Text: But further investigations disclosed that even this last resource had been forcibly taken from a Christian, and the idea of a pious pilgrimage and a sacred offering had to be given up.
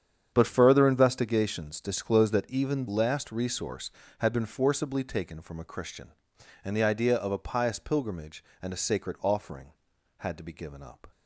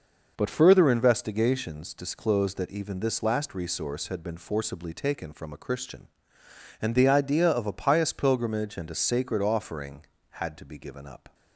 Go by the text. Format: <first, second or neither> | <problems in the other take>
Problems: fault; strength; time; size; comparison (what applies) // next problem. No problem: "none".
second | starts louder than the rest; strong; until 1.3 s; 8 dB // skips "this"; at 2.8 s